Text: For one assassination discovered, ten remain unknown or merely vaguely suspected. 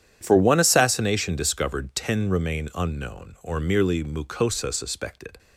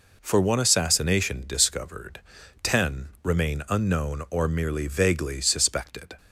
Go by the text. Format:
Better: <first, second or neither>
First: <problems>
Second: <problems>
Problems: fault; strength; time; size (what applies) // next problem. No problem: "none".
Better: second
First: starts louder than the rest; strong; until 1.2 s; 9 dB // says "mucosa" for "vaguely"; at 4.0 s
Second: none